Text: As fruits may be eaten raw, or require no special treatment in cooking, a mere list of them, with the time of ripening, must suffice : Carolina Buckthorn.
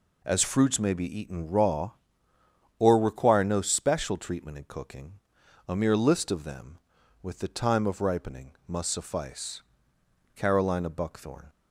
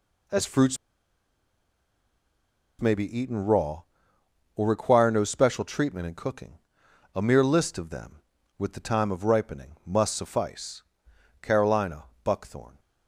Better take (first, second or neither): first